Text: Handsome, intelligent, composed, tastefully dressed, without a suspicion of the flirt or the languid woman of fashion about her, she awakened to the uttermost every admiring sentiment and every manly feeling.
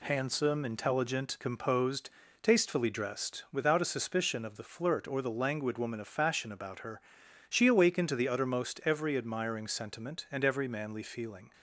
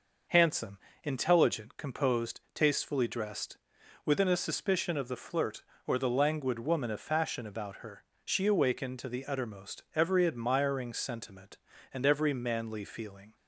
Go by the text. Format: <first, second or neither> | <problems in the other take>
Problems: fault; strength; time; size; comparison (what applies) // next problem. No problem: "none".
first | says "within" for "without"; at 4.0 s